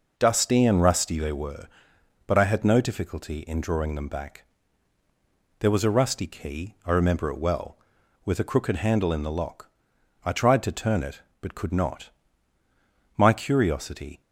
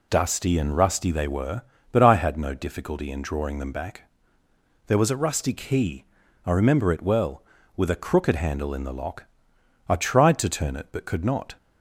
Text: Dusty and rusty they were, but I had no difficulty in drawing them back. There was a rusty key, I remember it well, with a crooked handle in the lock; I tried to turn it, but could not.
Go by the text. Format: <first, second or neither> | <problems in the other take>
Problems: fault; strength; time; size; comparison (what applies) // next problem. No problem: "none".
second | goes on to say "My curiosity"; noticeable; from 13.1 s on; 1.0 s long